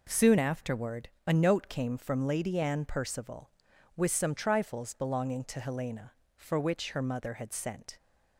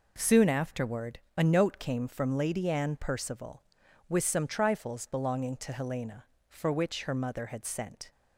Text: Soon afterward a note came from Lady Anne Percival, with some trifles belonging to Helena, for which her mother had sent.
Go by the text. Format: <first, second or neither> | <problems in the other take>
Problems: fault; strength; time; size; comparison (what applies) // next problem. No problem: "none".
neither | pauses between "afterward" and "a"; slight; the same in both